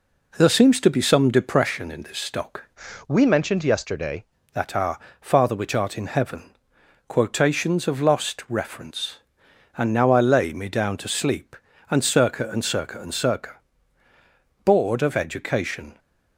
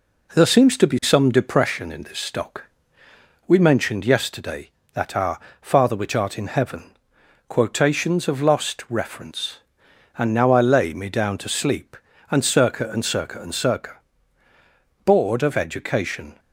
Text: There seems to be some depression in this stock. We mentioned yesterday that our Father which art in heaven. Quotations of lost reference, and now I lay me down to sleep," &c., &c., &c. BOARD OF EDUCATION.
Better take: second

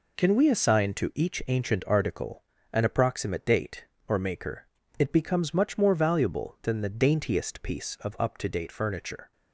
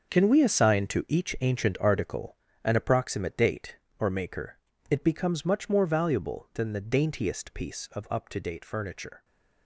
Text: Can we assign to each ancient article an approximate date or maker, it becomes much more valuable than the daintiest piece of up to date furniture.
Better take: first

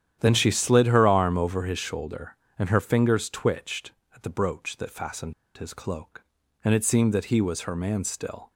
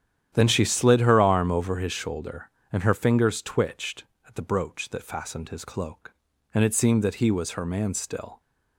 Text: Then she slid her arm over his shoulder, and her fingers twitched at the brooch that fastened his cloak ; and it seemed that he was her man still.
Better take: second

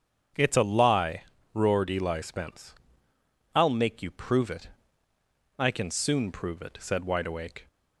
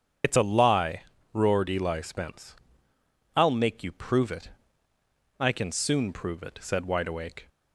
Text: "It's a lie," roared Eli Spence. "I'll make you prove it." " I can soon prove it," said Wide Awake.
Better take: first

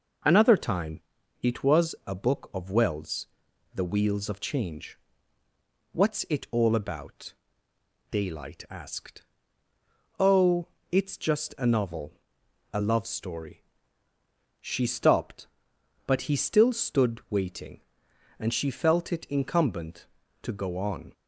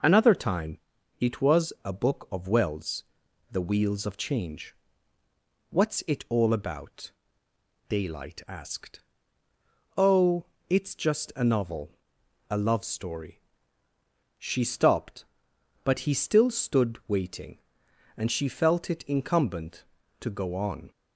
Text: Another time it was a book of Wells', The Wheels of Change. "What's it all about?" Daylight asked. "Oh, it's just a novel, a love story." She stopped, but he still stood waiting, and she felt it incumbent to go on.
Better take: neither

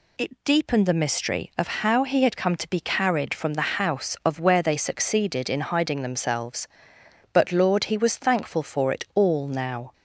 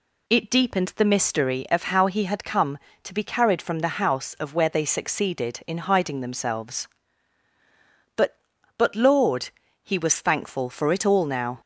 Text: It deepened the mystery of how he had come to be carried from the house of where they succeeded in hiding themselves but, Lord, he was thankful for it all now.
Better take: first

